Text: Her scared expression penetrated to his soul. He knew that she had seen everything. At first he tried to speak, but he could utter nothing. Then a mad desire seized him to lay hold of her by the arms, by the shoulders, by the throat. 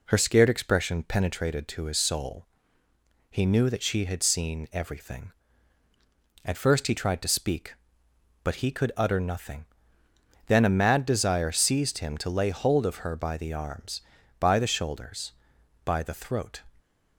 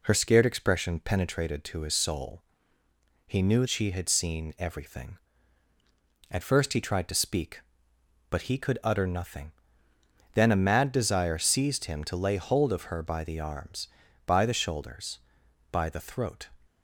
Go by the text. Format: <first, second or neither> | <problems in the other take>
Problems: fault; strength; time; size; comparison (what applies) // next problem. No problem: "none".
first | skips "that"; at 3.6 s